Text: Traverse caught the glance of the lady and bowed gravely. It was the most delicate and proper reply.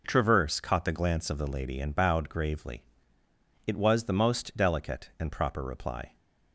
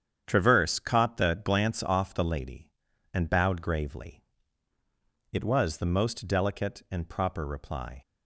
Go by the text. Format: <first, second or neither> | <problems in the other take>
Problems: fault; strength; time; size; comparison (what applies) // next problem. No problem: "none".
first | starts louder than the rest; strong; until 1.2 s; 8.5 dB // says "off" for "of"; at 1.8 s